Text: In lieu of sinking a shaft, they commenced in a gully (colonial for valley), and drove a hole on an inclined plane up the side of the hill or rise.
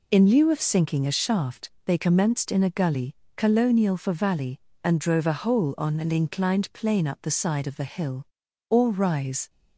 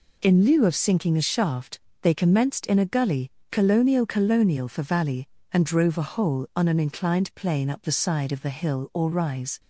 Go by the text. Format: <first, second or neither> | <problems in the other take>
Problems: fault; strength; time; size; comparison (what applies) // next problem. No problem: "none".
first | says "colonial" twice; at 4.0 s